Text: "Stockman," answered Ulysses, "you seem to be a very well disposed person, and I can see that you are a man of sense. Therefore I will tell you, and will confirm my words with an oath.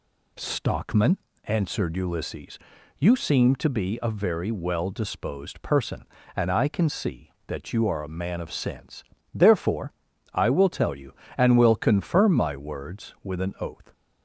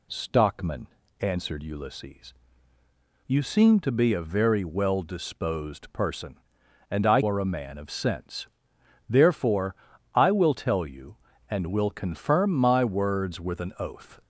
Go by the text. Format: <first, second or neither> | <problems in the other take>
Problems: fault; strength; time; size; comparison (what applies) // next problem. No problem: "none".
first | skips "can see that you"; at 7.2 s // pauses between "Therefore" and "I"; at 9.7 s; 0.38 s long; also in the first